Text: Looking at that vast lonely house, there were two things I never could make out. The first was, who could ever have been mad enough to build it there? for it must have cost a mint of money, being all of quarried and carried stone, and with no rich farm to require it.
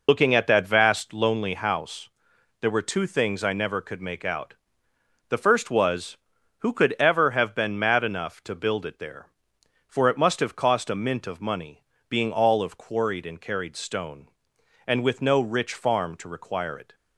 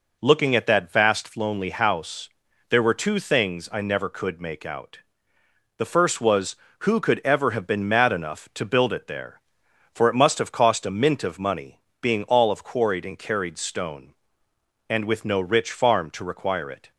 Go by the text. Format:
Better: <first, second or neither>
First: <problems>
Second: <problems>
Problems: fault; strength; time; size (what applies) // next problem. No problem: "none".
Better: second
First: loses the start of "Looking"; at 0.0 s; 60 ms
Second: none